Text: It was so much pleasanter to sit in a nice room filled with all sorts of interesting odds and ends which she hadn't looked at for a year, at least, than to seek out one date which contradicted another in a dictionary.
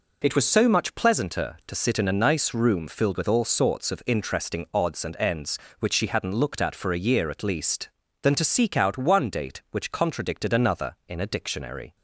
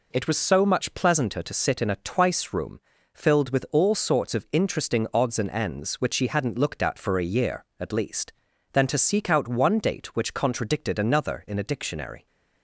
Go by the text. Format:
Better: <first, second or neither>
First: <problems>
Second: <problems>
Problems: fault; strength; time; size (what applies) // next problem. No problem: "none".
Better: first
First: none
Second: says "twice" for "nice"; at 1.9 s // pauses between "room" and "filled"; slight; at 2.8 s; 0.32 s long